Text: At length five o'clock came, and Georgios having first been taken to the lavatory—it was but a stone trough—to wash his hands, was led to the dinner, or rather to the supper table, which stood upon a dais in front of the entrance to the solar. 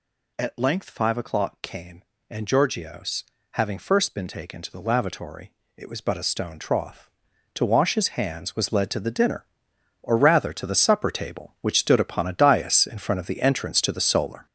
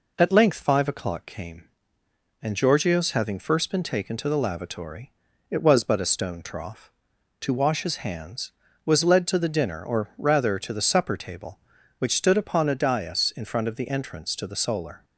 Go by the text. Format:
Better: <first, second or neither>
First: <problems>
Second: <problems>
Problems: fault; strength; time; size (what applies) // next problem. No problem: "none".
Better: second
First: gets louder; strong; throughout; 8 dB // pauses between "Georgios" and "having"; slight; at 3.2 s; 0.28 s long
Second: none